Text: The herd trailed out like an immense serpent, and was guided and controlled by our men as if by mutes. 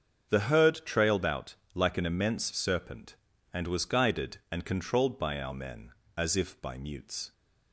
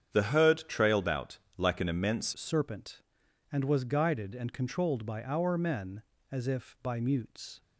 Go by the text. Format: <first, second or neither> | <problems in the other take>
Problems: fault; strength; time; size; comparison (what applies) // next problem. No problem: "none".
first | starts louder than the rest; strong; until 1.1 s; 8.5 dB; strong in the first // pauses between "out" and "like"; slight; at 1.3 s; 0.22 s long; slight in the first // changes voice at "serpent"; from 2.3 s on; 5.3 s long